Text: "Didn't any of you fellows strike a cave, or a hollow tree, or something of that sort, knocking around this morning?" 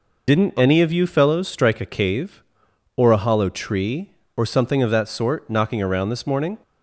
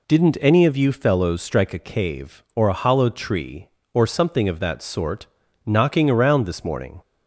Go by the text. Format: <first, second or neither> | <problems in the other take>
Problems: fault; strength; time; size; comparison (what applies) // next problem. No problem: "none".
second | loses the start of "Didn't"; at 0.2 s; 30 ms